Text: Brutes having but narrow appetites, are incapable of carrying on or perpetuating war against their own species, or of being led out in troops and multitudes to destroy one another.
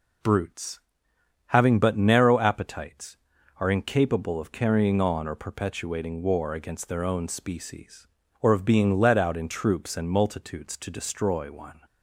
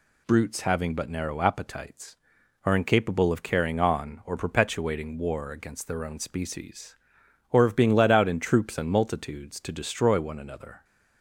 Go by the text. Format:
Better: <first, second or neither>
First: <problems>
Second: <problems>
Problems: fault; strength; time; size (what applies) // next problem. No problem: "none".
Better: second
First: pauses between "Brutes" and "having"; noticeable; at 0.7 s; 0.68 s long // stops before "another"; at 11.8 s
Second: none